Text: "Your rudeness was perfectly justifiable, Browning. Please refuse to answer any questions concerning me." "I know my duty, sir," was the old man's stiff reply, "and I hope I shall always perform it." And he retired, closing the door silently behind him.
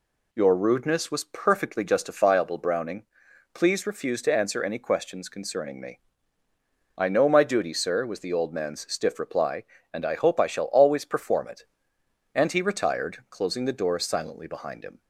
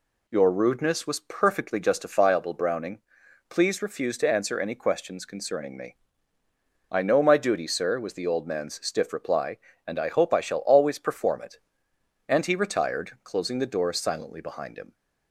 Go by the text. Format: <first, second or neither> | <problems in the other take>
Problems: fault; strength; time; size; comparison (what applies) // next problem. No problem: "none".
neither | none